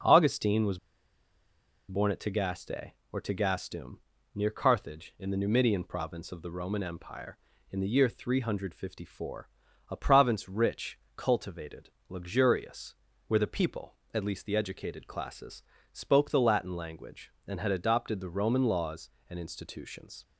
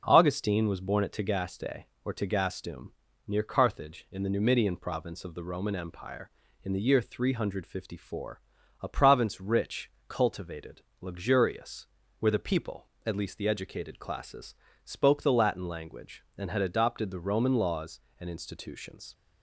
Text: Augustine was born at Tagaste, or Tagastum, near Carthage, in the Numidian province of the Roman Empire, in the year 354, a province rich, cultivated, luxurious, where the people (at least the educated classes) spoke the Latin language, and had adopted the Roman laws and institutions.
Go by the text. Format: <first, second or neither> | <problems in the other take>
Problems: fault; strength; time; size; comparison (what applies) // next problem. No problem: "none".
second | starts louder than the rest; until 2.1 s; 6 dB; noticeable in the second // pauses between "was" and "born"; at 0.7 s; 1.1 s long